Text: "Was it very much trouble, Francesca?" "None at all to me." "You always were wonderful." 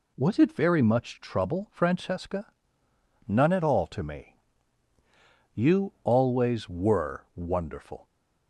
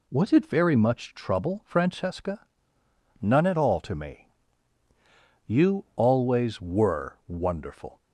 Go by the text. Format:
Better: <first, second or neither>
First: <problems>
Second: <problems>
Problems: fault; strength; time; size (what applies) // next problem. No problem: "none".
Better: neither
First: none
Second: none